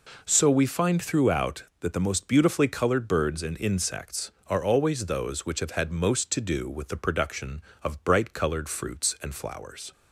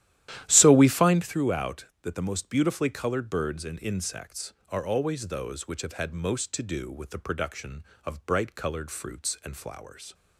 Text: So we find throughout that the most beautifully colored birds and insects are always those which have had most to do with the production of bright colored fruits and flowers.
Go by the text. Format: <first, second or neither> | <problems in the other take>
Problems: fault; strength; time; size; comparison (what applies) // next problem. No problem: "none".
first | starts louder than the rest; strong; until 1.3 s; 12.5 dB